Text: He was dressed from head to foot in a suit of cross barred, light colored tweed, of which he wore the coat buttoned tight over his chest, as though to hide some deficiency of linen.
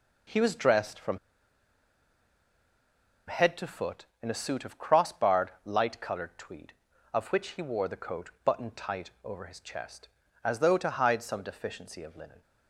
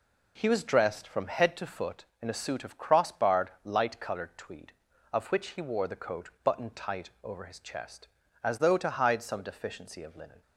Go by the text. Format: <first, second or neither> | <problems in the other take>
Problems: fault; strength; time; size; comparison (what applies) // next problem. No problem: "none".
second | pauses between "from" and "head"; strong; at 1.1 s; 2.1 s long // pauses between "coat" and "buttoned"; slight; at 8.2 s; 0.16 s long; slight in the second // pauses between "tight" and "over"; slight; at 9.0 s; 0.16 s long; slight in the second